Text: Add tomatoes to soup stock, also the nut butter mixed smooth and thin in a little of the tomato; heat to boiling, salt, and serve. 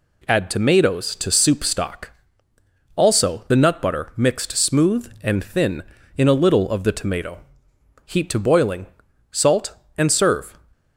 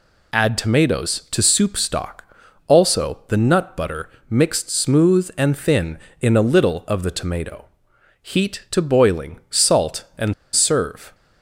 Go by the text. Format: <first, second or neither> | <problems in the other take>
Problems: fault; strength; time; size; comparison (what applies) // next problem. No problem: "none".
first | pauses between "butter" and "mixed"; slight; at 4.0 s; 0.20 s long // pauses between "and" and "serve"; slight; at 10.3 s; 0.20 s long